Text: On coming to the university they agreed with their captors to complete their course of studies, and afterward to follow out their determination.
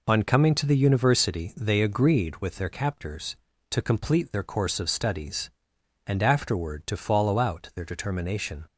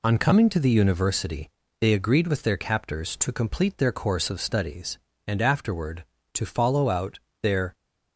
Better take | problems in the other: first | pauses between "university" and "they"; slight; at 1.4 s; 0.30 s long // pauses between "out" and "their"; slight; at 7.1 s; 0.24 s long // stops before "determination"; at 7.7 s

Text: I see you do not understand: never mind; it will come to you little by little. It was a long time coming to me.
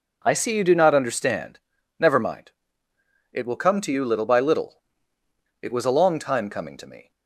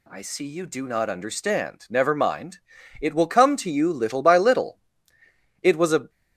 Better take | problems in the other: first | stops before "long time coming to me"; at 6.0 s

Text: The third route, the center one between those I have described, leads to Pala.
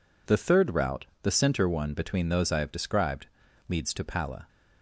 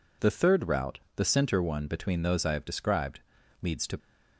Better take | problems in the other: first | stops before "Pala"; at 3.9 s

